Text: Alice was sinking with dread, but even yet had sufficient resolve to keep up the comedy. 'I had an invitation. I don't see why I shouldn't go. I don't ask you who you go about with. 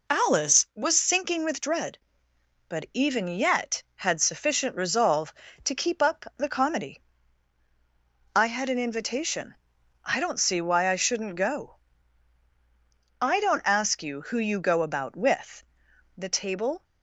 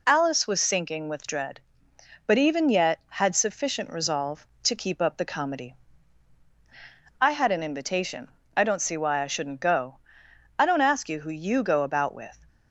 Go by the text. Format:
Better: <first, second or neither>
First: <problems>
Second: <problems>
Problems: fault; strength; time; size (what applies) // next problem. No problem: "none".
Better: second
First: goes on to say "The table"; noticeable; from 16.1 s on; 0.66 s long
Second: none